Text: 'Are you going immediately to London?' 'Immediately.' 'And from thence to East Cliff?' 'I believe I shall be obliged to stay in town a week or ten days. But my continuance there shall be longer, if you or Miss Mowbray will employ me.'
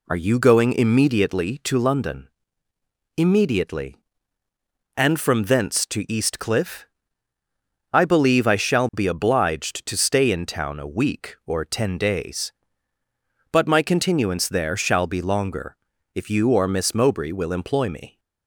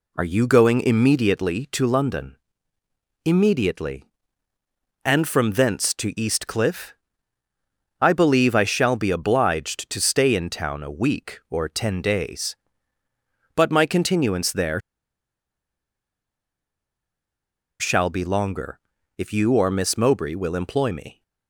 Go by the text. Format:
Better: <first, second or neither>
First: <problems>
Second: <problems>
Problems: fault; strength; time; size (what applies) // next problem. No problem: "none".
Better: first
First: none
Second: pauses between "there" and "shall"; strong; at 14.7 s; 3.0 s long